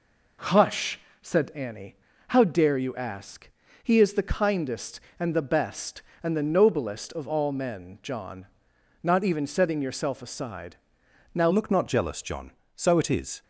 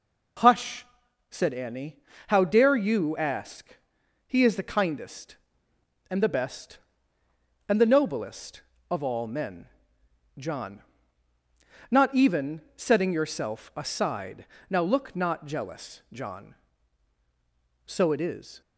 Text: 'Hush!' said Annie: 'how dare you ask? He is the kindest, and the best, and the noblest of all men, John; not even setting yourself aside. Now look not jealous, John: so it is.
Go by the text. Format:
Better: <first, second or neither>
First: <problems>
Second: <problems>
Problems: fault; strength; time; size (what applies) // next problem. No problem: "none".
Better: second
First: changes voice at "look"; from 11.5 s on; 1.9 s long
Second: none